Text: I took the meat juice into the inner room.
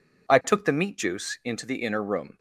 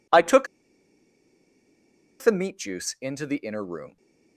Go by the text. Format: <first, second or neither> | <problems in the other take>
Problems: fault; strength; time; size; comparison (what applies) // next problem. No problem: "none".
first | pauses between "took" and "the"; strong; at 0.4 s; 1.7 s long